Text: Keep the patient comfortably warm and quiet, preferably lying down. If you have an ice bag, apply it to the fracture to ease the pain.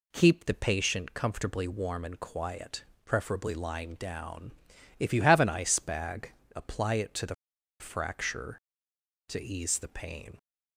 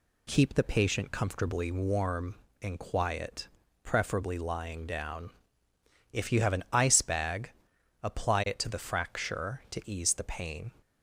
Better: second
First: pauses between "the" and "fracture"; at 7.3 s; 0.45 s long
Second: none

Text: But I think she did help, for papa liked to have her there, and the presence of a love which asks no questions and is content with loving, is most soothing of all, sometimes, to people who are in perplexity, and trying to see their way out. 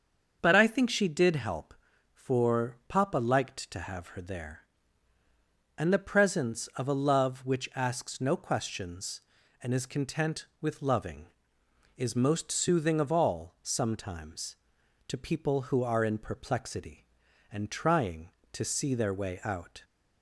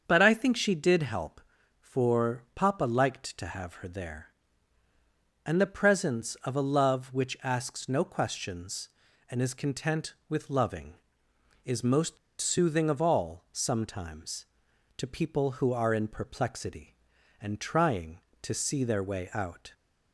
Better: first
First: starts louder than the rest; until 1.4 s; 6.5 dB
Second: starts louder than the rest; strong; until 1.0 s; 7 dB // pauses between "most" and "soothing"; slight; at 12.1 s; 0.24 s long

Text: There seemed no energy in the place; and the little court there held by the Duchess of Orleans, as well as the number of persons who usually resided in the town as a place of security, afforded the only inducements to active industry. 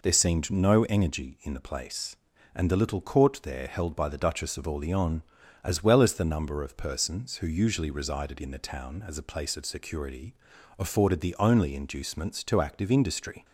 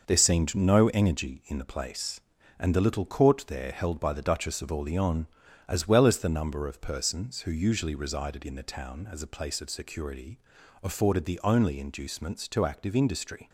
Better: first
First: none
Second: gets quieter; strong; throughout; 7 dB

